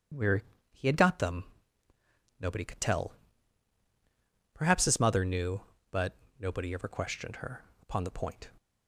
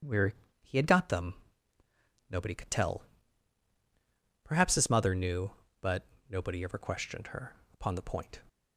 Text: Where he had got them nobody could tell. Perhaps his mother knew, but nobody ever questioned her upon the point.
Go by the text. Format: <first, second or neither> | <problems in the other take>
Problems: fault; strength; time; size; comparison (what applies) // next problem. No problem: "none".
neither | pauses between "Where" and "he"; slight; the same in both // pauses between "them" and "nobody"; noticeable; the same in both // pauses between "but" and "nobody"; slight; the same in both // pauses between "her" and "upon"; slight; the same in both